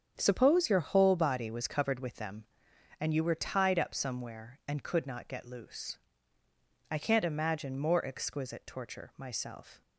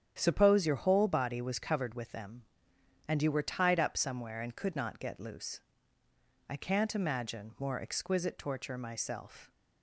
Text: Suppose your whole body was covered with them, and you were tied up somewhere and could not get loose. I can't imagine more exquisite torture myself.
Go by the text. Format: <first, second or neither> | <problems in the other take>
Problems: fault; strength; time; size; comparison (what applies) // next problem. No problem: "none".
neither | starts louder than the rest; strong; the same in both